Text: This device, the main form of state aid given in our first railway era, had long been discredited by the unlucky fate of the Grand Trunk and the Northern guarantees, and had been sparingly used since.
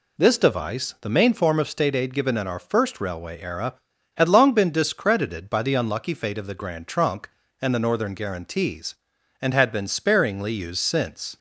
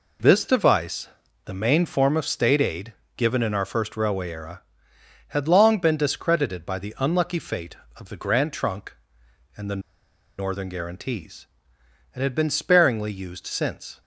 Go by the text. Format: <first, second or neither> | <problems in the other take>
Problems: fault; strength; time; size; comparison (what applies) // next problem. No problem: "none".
first | pauses between "aid" and "given"; slight; at 2.9 s; 0.24 s long // pauses between "the" and "Northern"; noticeable; at 9.8 s; 0.57 s long